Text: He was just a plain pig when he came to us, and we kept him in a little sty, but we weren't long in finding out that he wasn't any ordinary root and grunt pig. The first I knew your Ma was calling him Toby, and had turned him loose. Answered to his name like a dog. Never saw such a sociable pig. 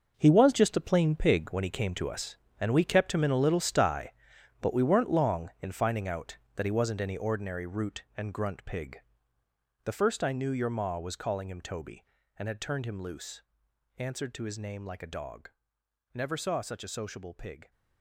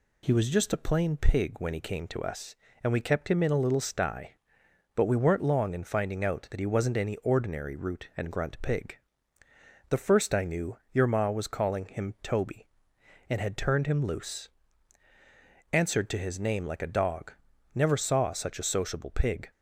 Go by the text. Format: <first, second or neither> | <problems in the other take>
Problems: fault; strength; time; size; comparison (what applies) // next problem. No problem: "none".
second | gets quieter; strong; throughout; 11.5 dB